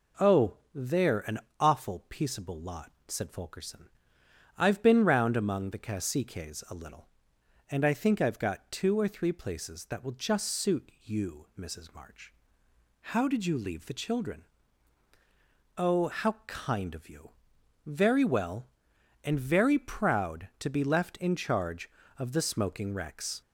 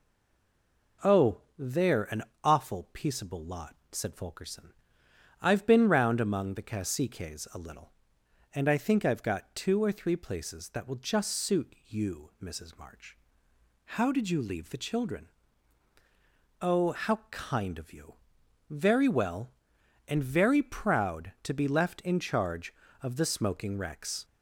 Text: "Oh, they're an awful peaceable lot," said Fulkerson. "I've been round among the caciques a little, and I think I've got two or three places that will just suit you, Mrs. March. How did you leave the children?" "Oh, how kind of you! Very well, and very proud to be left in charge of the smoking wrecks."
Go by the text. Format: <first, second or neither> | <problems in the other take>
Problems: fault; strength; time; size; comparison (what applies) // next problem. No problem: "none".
first | stays silent before the first word; until 1.0 s; 1.0 s long // pauses between "an" and "awful"; slight; at 2.2 s; 0.20 s long; slight in the first